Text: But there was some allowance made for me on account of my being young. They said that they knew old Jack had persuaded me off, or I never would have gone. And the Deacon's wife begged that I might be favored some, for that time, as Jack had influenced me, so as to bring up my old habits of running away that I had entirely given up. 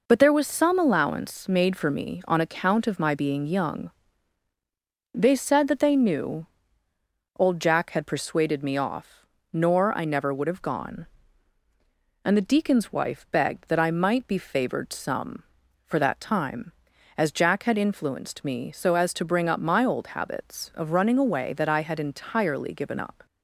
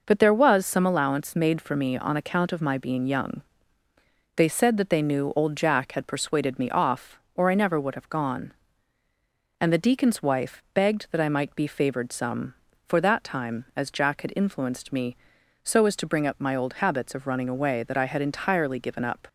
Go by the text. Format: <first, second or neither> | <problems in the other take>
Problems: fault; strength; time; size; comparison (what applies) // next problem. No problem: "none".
second | pauses between "knew" and "old"; noticeable; at 6.4 s; 0.92 s long // says "nor" for "or"; at 9.5 s